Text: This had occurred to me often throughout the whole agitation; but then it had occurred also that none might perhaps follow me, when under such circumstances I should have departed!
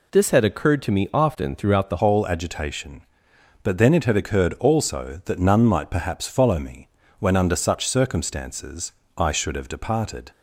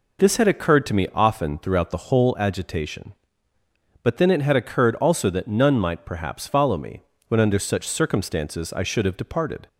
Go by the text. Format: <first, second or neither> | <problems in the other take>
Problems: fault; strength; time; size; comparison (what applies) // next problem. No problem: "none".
second | changes voice at "whole"; from 1.9 s on; 8.4 s long // pauses between "circumstances" and "I"; slight; at 8.9 s; 0.24 s long